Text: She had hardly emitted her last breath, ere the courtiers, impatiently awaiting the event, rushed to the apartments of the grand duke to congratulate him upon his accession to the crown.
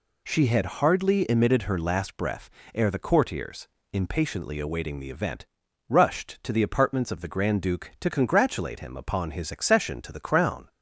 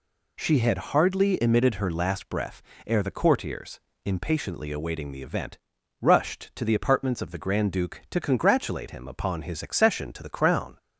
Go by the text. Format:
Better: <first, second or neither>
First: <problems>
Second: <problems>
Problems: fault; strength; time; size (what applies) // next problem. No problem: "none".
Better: neither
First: none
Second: none